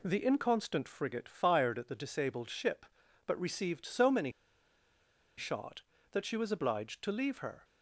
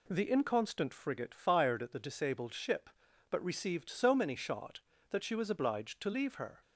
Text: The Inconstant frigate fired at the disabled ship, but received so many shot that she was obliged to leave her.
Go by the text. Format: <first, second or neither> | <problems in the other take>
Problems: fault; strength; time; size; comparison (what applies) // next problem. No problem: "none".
second | pauses between "many" and "shot"; at 4.3 s; 1.0 s long